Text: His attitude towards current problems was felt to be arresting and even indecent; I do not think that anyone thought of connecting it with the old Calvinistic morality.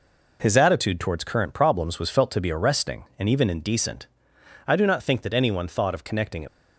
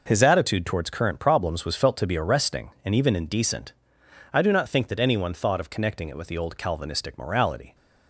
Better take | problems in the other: second | stops before "with the old Calvinistic morality"; at 6.4 s

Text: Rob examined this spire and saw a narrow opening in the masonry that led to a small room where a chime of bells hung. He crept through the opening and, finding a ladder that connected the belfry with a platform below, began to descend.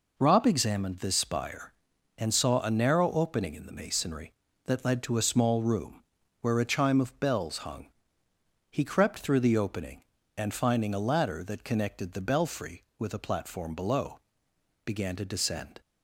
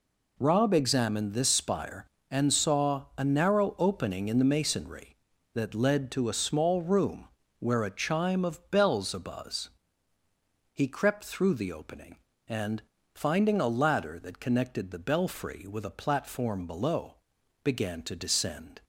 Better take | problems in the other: first | pauses between "room" and "where"; slight; at 7.2 s; 0.32 s long; slight in the first // says "abuzz" for "hung"; at 9.1 s

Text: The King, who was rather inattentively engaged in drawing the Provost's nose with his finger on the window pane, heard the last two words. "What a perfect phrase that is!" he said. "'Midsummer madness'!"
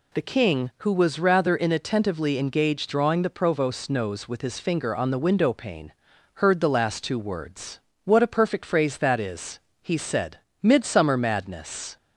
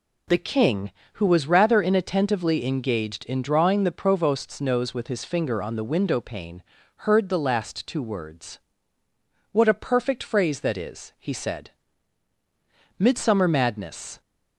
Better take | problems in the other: second | skips "in"; at 2.9 s

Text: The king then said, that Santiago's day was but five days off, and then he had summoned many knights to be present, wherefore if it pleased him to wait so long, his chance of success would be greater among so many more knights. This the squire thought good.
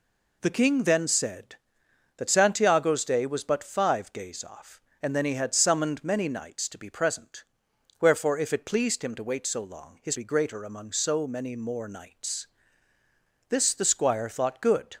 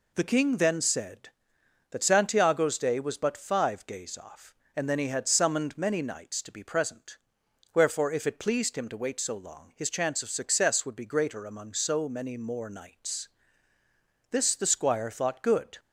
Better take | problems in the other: second | skips "chance of success would"; at 10.1 s

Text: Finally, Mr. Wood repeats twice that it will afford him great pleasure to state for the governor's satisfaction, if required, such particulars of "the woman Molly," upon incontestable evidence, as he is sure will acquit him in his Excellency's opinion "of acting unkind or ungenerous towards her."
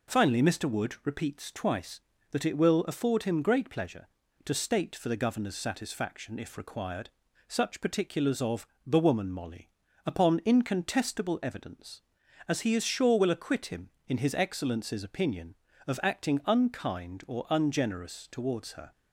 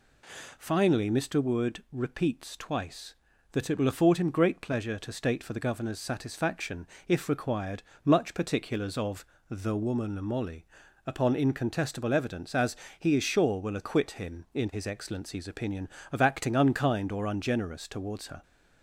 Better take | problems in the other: first | says "much" for "such"; at 8.0 s // pauses between "of" and "the"; slight; at 9.2 s; 0.24 s long; slight in the first // pauses between "as" and "he"; slight; at 12.7 s; 0.24 s long

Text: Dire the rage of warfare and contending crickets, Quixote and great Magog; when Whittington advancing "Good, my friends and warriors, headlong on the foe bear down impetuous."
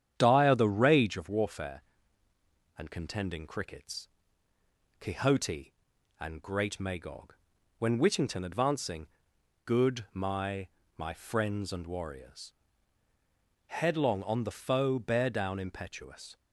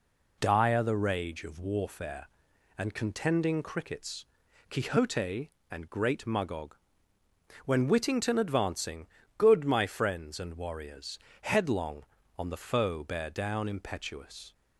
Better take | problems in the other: second | starts louder than the rest; strong; until 1.1 s; 9 dB // pauses between "advancing" and "Good"; noticeable; at 9.0 s; 0.58 s long; slight in the second // says "my" twice; at 10.9 s

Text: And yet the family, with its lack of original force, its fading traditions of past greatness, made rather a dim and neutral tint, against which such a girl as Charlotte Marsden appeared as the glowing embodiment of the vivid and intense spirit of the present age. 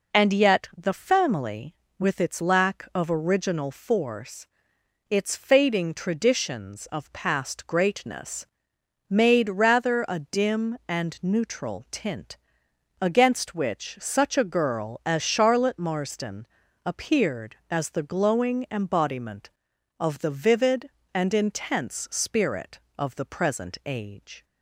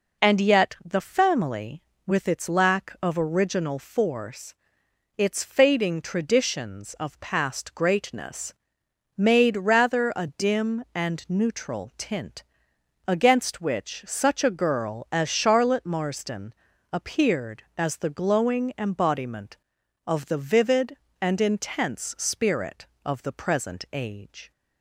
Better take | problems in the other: neither | pauses between "Marsden" and "appeared"; the same in both

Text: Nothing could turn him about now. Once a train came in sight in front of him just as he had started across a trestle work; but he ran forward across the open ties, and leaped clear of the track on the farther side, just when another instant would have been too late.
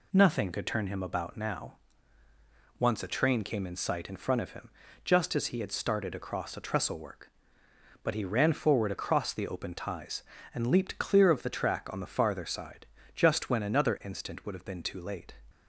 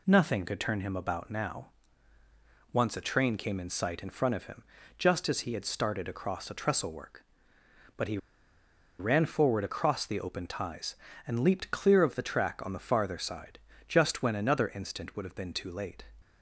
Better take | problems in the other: first | pauses between "him" and "just"; slight; at 4.6 s; 0.34 s long; slight in the first // pauses between "he" and "ran"; noticeable; at 8.1 s; 0.81 s long

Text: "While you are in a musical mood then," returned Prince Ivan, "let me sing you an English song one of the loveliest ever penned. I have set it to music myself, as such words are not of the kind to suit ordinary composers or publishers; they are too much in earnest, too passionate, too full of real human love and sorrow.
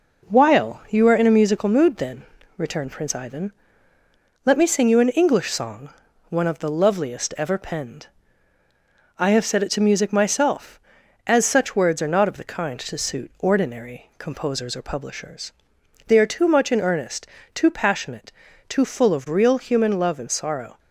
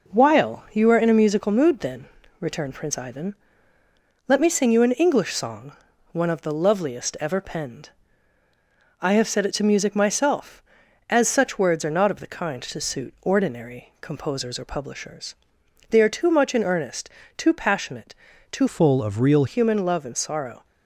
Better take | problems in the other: first | pauses between "song" and "one"; at 5.7 s; 0.38 s long; also in the first // changes voice from "full" to "real"; from 18.6 to 19.4 s; 0.8 s long

